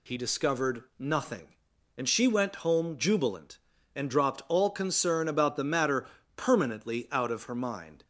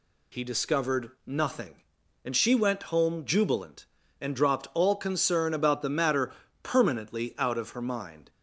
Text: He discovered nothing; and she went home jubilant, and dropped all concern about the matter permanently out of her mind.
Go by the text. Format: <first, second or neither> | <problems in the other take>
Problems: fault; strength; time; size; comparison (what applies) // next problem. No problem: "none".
neither | pauses between "discovered" and "nothing"; slight; the same in both // pauses between "matter" and "permanently"; slight; the same in both